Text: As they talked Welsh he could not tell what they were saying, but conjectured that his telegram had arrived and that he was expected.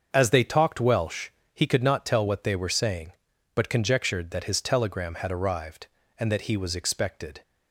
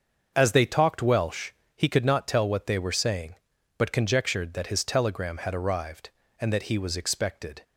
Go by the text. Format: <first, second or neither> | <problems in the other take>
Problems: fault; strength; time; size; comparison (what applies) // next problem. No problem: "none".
neither | starts louder than the rest; the same in both // pauses between "Welsh" and "he"; slight; the same in both